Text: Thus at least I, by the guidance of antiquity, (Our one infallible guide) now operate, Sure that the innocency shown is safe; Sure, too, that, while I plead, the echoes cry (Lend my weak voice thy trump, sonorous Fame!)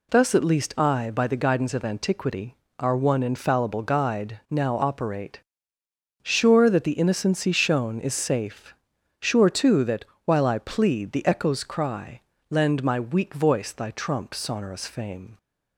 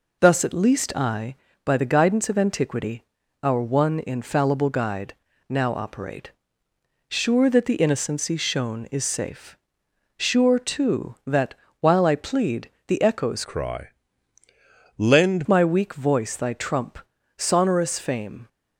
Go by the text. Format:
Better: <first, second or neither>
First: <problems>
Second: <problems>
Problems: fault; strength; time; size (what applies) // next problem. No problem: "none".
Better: first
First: none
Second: changes voice from "cry" to "Lend"; from 13.4 to 15.4 s; 2.0 s long